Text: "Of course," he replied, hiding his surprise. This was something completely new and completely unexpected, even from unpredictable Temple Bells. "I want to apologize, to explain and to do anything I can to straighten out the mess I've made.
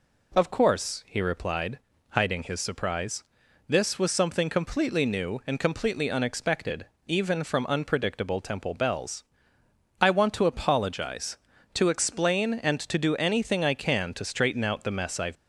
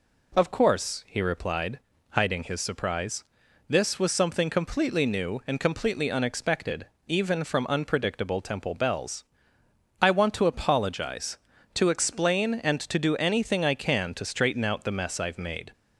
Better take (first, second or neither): second